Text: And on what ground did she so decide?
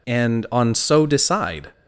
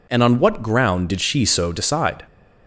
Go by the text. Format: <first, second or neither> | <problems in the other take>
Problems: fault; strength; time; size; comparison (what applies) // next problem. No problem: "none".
second | skips "what ground did she"; at 0.7 s